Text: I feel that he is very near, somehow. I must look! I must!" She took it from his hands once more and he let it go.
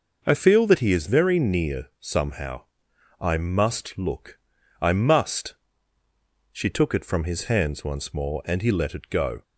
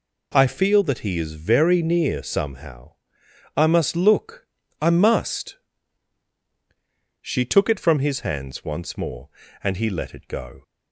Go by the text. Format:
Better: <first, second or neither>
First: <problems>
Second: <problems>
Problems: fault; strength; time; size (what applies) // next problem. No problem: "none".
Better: neither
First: none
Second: none